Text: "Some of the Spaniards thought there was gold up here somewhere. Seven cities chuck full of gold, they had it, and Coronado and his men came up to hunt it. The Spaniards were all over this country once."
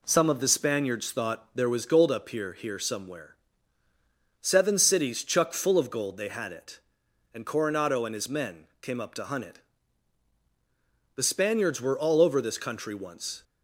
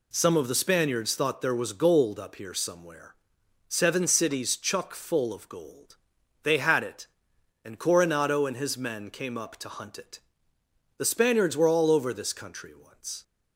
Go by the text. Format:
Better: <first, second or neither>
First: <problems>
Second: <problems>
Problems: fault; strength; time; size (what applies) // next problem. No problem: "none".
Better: second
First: says "here" twice; at 2.5 s // pauses between "men" and "came"; slight; at 8.6 s; 0.16 s long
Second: none